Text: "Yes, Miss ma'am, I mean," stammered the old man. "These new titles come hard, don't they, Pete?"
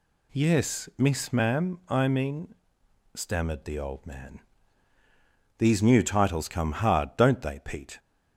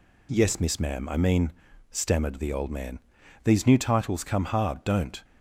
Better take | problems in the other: first | stops before "they Pete"; at 5.2 s

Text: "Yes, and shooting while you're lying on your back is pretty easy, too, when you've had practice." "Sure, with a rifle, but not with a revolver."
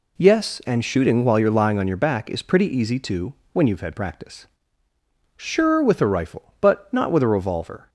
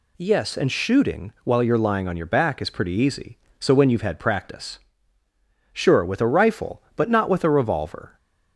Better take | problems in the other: first | says "so" for "too"; at 3.5 s

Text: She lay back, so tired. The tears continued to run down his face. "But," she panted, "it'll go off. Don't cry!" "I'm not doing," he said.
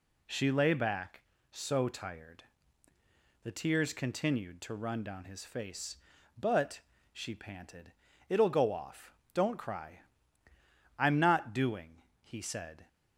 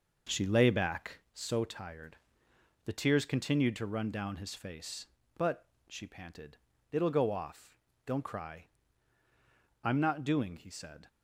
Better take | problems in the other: first | starts louder than the rest; noticeable; until 1.4 s; 5.5 dB

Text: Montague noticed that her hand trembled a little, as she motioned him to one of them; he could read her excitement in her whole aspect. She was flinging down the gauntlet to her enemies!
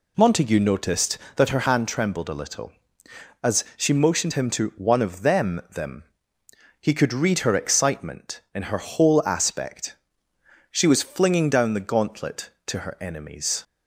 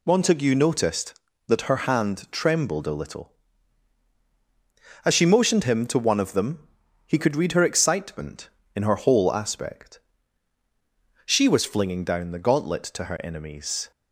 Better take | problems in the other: second | says "them" twice; at 5.7 s

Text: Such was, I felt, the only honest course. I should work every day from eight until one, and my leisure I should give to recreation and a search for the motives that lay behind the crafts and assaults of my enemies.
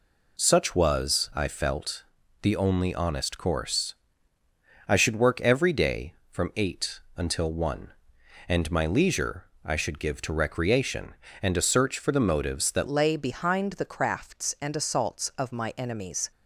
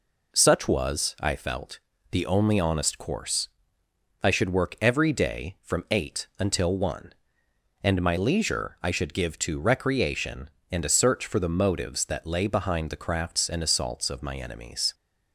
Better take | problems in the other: second | pauses between "eight" and "until"; slight; at 6.9 s; 0.18 s long // pauses between "leisure" and "I"; slight; at 9.4 s; 0.20 s long // changes voice at "lay"; from 12.8 s on; 3.5 s long

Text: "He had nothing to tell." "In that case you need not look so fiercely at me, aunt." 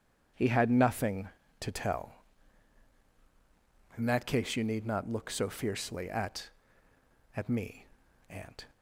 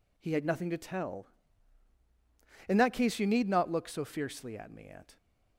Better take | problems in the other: second | says "at" twice; at 7.3 s

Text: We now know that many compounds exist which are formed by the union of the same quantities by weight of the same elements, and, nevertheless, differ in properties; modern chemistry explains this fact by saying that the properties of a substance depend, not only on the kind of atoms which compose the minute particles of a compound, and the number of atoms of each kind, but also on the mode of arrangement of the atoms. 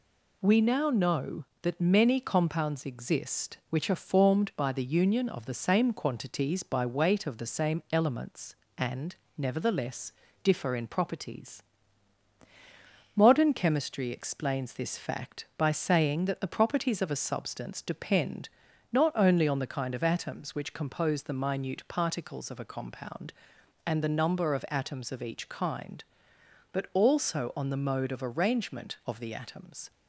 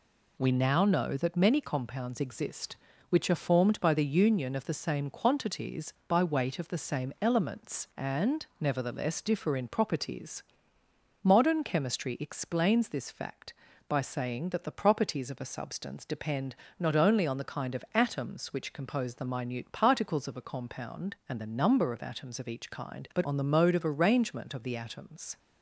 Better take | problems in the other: first | skips "also"; at 23.2 s

